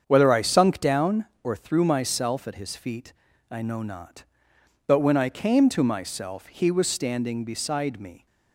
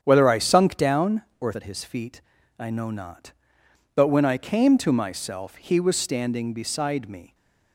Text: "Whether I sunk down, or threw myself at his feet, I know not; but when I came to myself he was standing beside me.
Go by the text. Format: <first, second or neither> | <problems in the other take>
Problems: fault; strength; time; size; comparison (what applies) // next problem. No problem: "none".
first | starts louder than the rest; strong; until 1.0 s; 8 dB; strong in the first // skips "threw myself"; at 1.5 s